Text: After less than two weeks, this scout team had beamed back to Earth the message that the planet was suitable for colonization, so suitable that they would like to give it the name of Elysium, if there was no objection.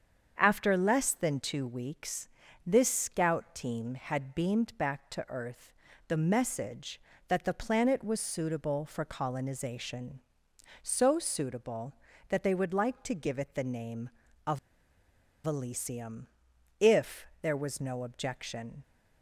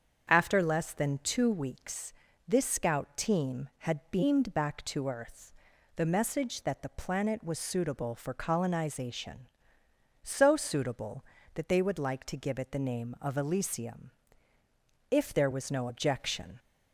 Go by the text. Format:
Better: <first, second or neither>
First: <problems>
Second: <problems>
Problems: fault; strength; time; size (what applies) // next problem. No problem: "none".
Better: second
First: starts louder than the rest; strong; until 1.3 s; 7 dB // pauses between "Earth" and "the"; slight; at 5.7 s; 0.36 s long // pauses between "of" and "Elysium"; noticeable; at 14.5 s; 0.87 s long // pauses between "if" and "there"; slight; at 17.2 s; 0.16 s long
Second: starts louder than the rest; strong; until 1.3 s; 7.5 dB // pauses between "Earth" and "the"; at 5.5 s; 0.44 s long